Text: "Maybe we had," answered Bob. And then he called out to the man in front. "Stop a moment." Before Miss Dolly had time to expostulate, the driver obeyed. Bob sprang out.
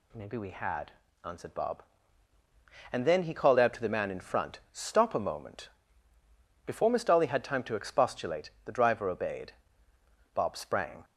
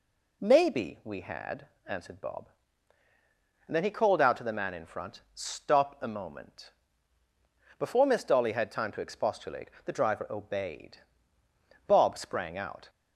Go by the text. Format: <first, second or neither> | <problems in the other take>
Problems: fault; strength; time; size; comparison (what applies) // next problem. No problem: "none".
second | stops before "out"; at 11.0 s